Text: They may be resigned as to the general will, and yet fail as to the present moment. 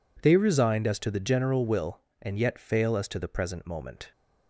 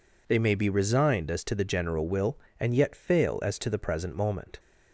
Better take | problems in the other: second | skips "may be"; at 0.3 s

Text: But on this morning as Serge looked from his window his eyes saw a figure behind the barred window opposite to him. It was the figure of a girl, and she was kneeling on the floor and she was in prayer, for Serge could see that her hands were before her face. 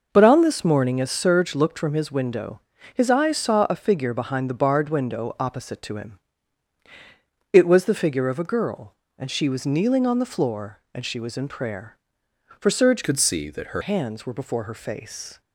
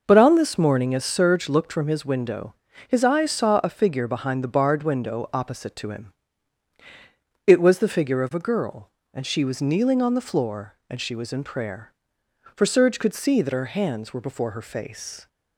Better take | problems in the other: second | pauses between "window" and "his"; slight; at 2.6 s; 0.34 s long; slight in the second // changes voice from "could" to "her"; from 13.0 to 13.8 s; 0.8 s long

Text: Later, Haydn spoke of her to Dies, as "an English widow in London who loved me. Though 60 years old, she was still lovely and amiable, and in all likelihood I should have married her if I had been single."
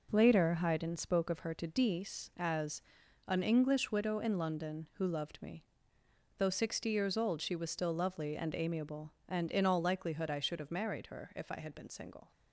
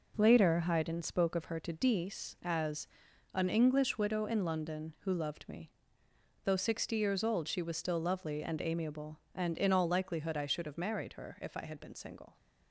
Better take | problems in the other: neither | pauses between "as" and "an"; the same in both

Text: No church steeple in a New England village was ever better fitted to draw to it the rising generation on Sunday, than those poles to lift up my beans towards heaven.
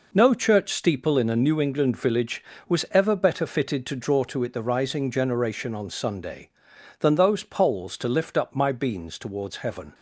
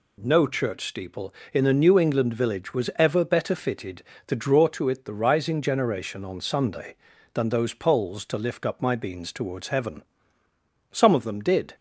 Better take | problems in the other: first | goes on to say "Some of them did"; noticeable; from 10.9 s on; 0.84 s long

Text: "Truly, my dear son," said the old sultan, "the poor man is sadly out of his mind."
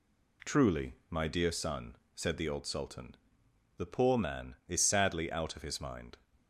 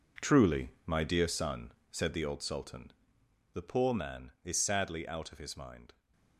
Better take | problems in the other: first | gets quieter; strong; throughout; 10.5 dB

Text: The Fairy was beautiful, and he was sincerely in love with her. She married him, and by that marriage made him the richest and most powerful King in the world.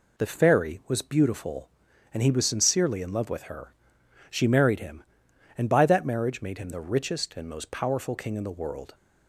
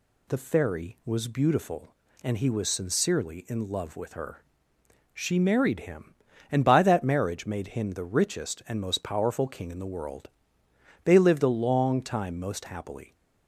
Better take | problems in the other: first | goes on to say "They lived a long time most happily"; strong; from 11.0 s on; 2.0 s long

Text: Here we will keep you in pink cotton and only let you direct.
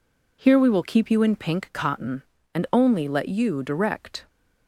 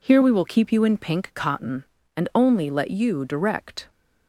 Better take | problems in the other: neither | none

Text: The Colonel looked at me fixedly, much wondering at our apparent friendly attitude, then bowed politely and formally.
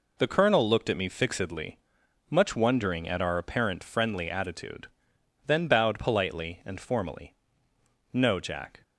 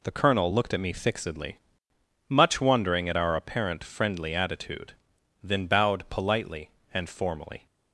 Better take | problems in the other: second | goes on to say "No Jack"; noticeable; from 8.1 s on; 0.70 s long

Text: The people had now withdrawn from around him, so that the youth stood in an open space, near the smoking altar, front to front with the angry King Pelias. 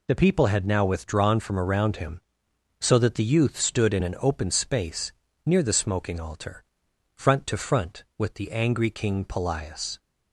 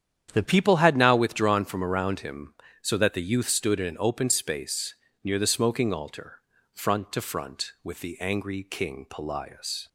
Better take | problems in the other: first | starts louder than the rest; strong; until 1.3 s; 9 dB // changes voice at "people"; from 0.4 s on; 9.4 s long

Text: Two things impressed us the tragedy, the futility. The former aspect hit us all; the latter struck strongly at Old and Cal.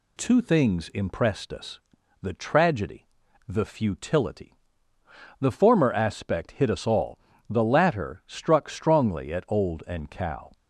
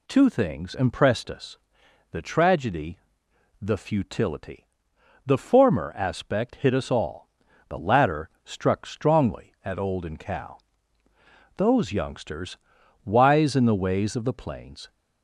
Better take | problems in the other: first | pauses between "us" and "the"; noticeable; at 1.5 s; 0.54 s long; also in the first // pauses between "latter" and "struck"; slight; at 8.2 s; 0.16 s long // goes on to say "Those youngsters wise in the ways of the plains"; strong; from 11.5 s on; 3.3 s long

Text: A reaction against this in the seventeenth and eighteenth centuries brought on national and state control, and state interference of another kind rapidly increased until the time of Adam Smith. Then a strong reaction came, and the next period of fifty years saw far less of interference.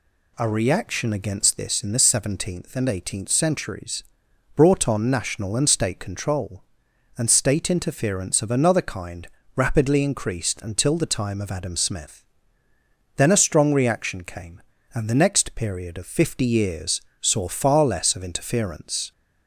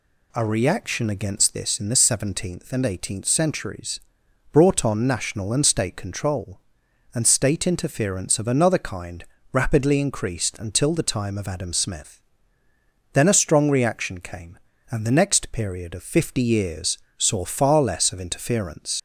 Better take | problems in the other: first | pauses between "centuries" and "brought"; noticeable; at 3.9 s; 0.54 s long; noticeable in the first // pauses between "kind" and "rapidly"; slight; at 9.2 s; 0.28 s long; slight in the first // pauses between "years" and "saw"; slight; at 16.9 s; 0.20 s long; slight in the first // leaves "interference" unfinished; at 18.9 s; 85 ms

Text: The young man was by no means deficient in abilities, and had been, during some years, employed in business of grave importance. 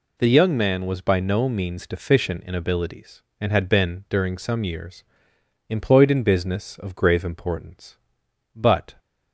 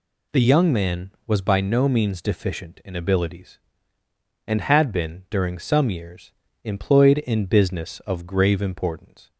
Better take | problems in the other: second | goes on to say "But"; slight; from 8.5 s on; 0.40 s long

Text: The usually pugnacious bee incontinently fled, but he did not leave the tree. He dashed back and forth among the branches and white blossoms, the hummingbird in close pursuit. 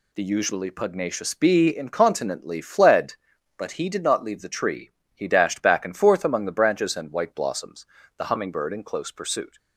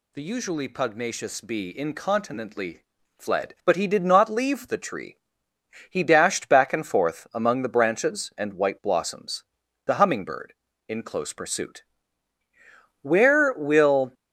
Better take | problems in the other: first | pauses between "incontinently" and "fled"; at 2.8 s; 0.38 s long // goes on to say "Where will"; noticeable; from 13.0 s on; 1.1 s long

